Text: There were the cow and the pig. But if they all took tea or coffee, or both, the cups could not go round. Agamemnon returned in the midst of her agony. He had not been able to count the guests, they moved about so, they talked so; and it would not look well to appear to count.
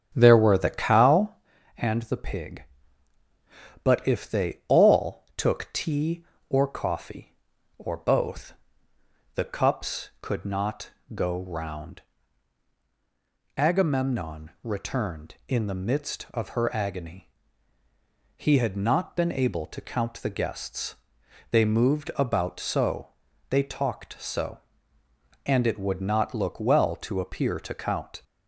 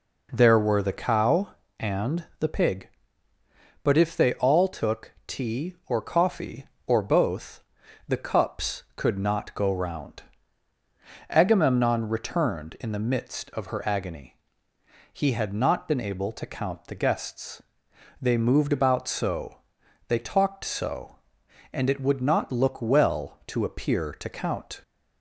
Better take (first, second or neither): second